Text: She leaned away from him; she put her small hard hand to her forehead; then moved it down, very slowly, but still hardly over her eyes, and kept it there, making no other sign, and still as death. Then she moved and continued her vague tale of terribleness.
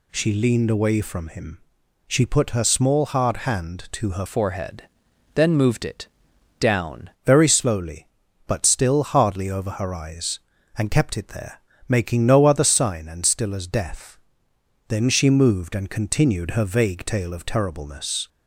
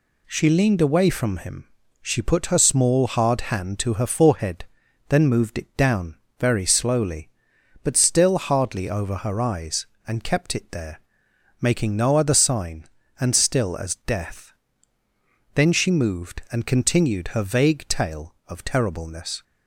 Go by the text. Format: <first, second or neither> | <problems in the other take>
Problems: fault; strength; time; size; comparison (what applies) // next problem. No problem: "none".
second | changes voice from "forehead" to "down"; from 4.2 to 7.0 s; 2.8 s long // pauses between "it" and "down"; noticeable; at 6.0 s; 0.52 s long